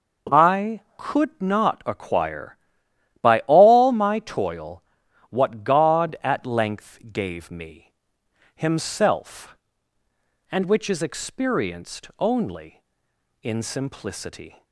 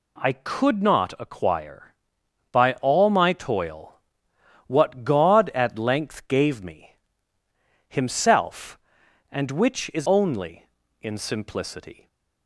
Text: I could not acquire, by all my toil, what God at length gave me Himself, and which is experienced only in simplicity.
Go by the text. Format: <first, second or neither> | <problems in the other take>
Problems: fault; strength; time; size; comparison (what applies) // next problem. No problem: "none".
first | pauses between "me" and "Himself"; noticeable; at 6.9 s; 0.92 s long; noticeable in the first // skips "experienced"; at 10.0 s